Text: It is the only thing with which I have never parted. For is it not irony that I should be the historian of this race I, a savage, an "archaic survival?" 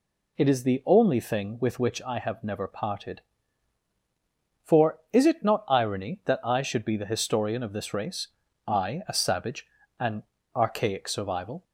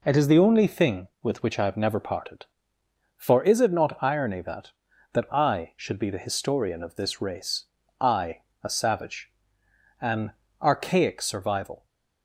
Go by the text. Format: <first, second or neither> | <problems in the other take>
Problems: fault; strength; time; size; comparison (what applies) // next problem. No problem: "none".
first | says "that" twice; at 5.1 s // pauses between "race" and "I"; slight; at 7.6 s; 0.36 s long; also in the first // pauses between "an" and "archaic"; slight; at 10.3 s; 0.28 s long; slight in the first